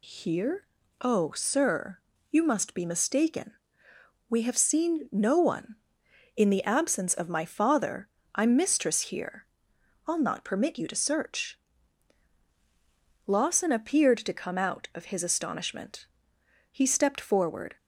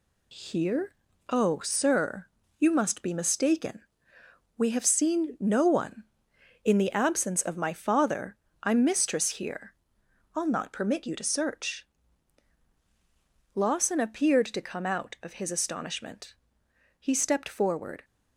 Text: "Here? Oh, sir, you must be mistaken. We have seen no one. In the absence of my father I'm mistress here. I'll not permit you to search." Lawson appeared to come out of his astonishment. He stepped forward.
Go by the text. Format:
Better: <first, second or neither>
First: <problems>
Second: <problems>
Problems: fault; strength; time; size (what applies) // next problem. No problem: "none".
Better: first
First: pauses between "father" and "I'm"; slight; at 8.0 s; 0.24 s long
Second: gets quieter; noticeable; throughout; 5.5 dB // pauses between "father" and "I'm"; slight; at 8.3 s; 0.24 s long